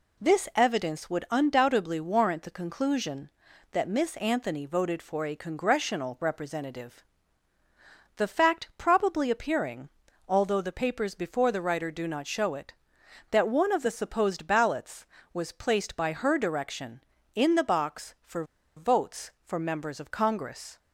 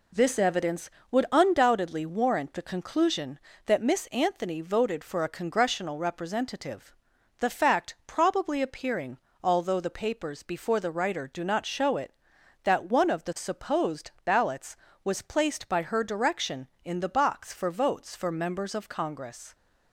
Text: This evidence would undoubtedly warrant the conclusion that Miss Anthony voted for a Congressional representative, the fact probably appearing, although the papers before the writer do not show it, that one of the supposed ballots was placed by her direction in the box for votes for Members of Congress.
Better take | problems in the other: second | pauses between "for" and "votes"; slight; at 18.4 s; 0.32 s long

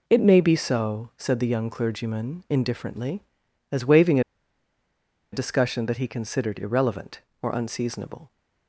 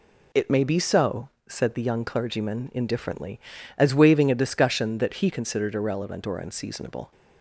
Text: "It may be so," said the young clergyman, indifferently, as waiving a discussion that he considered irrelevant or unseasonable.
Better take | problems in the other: second | pauses between "waiving" and "a"; at 4.1 s; 1.1 s long

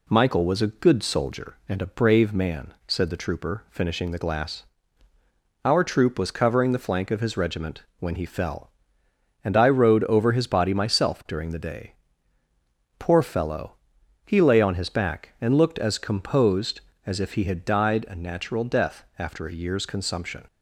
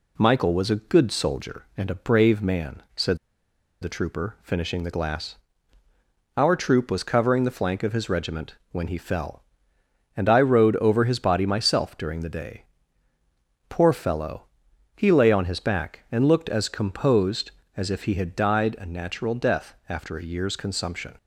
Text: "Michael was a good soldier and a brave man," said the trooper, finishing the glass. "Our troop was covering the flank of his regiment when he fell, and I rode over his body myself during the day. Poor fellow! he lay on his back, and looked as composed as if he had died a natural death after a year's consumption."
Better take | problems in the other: first | pauses between "said" and "the"; noticeable; at 3.1 s; 0.64 s long // pauses between "regiment" and "when"; slight; at 8.5 s; 0.16 s long; slight in the first

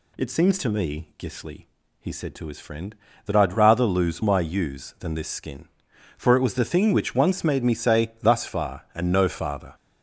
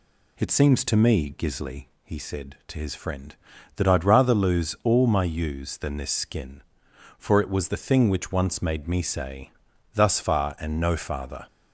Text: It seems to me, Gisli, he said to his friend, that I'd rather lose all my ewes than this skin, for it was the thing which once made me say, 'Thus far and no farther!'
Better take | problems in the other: second | skips "all"; at 4.2 s

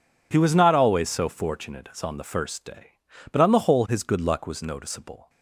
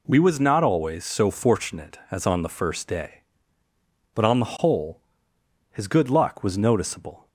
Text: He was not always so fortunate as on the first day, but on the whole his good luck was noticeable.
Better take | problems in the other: first | says "We" for "He"; at 0.0 s // pauses between "whole" and "his"; noticeable; at 5.0 s; 0.70 s long

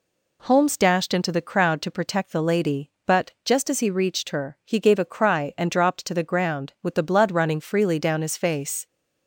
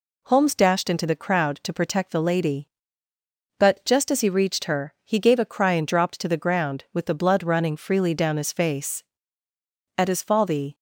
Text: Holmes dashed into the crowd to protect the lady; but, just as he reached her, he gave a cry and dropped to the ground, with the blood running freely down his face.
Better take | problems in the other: first | goes on to say "At his fall the"; noticeable; from 9.9 s on; 0.78 s long

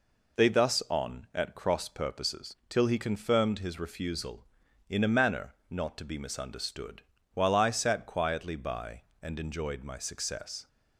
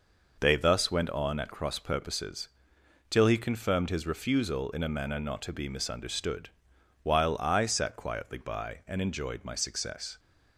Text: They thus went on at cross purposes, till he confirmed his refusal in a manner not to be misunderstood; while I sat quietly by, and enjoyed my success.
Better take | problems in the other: second | skips "went"; at 0.8 s // pauses between "manner" and "not"; slight; at 5.5 s; 0.16 s long

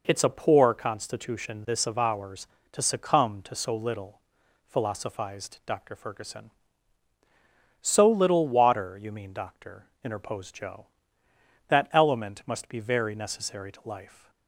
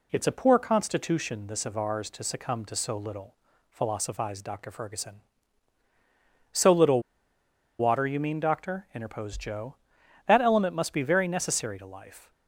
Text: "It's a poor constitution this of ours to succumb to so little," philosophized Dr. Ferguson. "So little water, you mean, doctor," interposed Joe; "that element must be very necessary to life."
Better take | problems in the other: first | pauses between "little" and "water"; noticeable; at 6.9 s; 0.79 s long

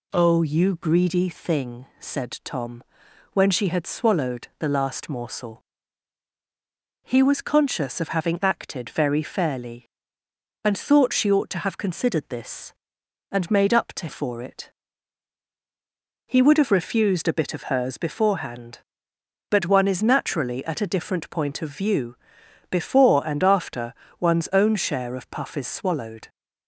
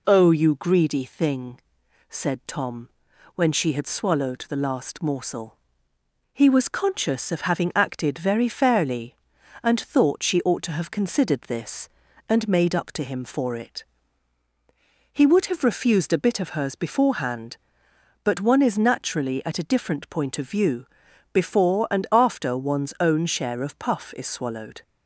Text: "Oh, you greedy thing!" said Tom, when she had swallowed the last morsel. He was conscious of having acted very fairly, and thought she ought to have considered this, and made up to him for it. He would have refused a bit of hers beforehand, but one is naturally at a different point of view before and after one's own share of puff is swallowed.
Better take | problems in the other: second | skips "him"; at 14.0 s // pauses between "view" and "before"; noticeable; at 22.1 s; 0.54 s long; noticeable in the second // pauses between "after" and "one's"; slight; at 23.9 s; 0.26 s long

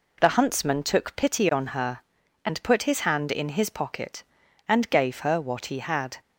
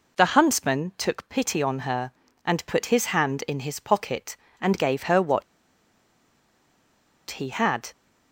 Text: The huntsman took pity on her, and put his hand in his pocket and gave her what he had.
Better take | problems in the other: first | pauses between "what" and "he"; strong; at 5.4 s; 1.8 s long

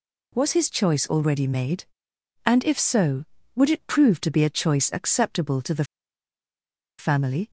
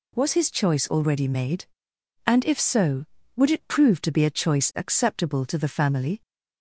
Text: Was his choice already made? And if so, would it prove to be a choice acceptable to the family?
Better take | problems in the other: second | pauses between "the" and "family"; at 5.8 s; 1.1 s long

